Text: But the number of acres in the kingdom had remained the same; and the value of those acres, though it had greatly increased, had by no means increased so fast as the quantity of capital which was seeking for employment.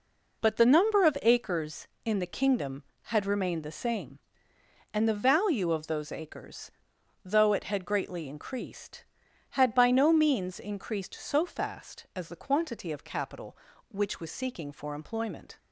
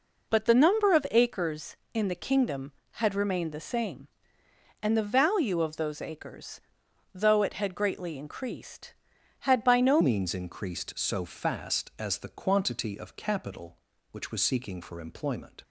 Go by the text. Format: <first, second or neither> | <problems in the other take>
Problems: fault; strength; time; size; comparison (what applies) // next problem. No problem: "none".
first | changes voice at "means"; from 10.0 s on; 5.6 s long